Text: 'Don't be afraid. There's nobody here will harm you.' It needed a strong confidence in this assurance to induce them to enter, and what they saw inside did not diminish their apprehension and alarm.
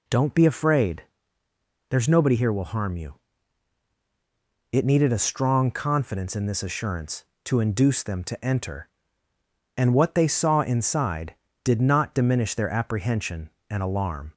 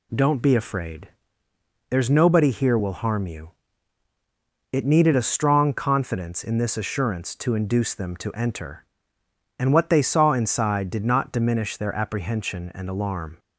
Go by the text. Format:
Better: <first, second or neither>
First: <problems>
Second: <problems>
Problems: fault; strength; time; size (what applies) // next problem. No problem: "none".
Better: neither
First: none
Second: none